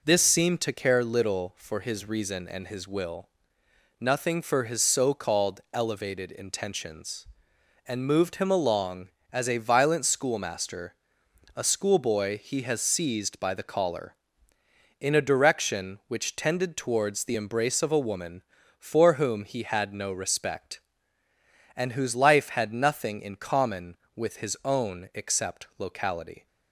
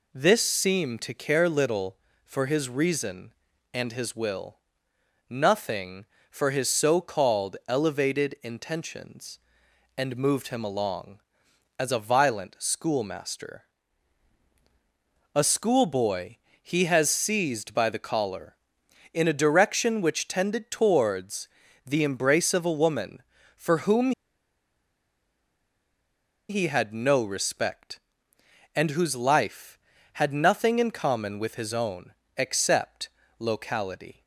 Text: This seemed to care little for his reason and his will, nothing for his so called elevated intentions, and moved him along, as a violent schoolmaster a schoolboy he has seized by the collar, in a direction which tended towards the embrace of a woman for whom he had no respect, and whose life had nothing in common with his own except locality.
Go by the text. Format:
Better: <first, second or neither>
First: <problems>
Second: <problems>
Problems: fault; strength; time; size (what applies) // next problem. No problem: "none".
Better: first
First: pauses between "schoolmaster" and "a"; noticeable; at 10.9 s; 0.62 s long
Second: pauses between "schoolmaster" and "a"; strong; at 13.6 s; 1.6 s long // pauses between "schoolboy" and "he"; slight; at 16.3 s; 0.26 s long // pauses between "towards" and "the"; at 21.4 s; 0.40 s long // pauses between "whom" and "he"; strong; at 24.1 s; 2.3 s long // pauses between "own" and "except"; slight; at 32.1 s; 0.26 s long // pauses between "except" and "locality"; slight; at 33.0 s; 0.32 s long